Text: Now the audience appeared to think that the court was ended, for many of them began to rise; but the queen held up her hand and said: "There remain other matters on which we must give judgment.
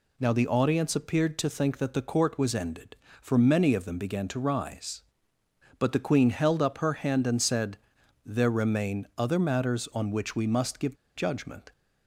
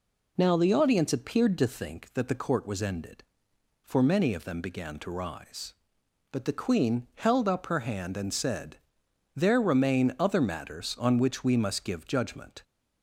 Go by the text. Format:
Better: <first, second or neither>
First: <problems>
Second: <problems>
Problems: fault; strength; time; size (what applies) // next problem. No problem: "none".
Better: second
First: pauses between "give" and "judgment"; slight; at 10.9 s; 0.19 s long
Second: none